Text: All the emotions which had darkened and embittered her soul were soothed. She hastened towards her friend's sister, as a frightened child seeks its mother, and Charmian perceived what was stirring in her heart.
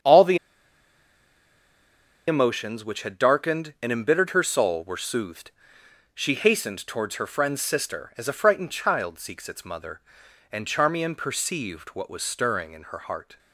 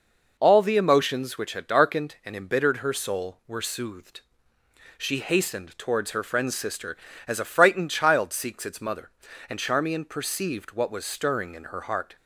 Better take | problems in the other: second | starts louder than the rest; strong; until 2.9 s; 7.5 dB // pauses between "the" and "emotions"; strong; at 0.3 s; 1.9 s long

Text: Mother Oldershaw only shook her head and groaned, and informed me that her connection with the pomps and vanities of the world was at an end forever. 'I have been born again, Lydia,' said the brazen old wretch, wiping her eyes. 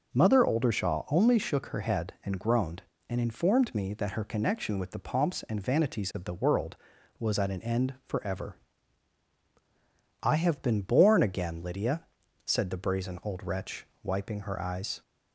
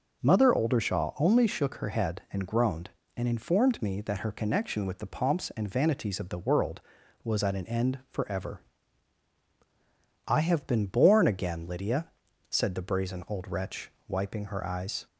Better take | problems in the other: neither | none

